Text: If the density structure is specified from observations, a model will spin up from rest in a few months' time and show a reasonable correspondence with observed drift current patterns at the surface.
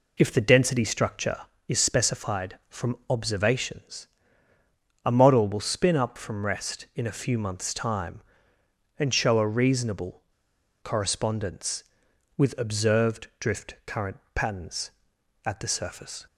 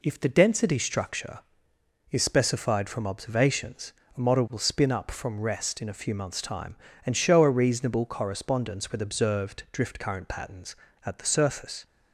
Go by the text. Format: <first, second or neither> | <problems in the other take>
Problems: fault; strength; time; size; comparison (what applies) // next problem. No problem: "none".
second | pauses between "reasonable" and "correspondence"; noticeable; at 10.2 s; 0.59 s long // pauses between "current" and "patterns"; slight; at 14.1 s; 0.16 s long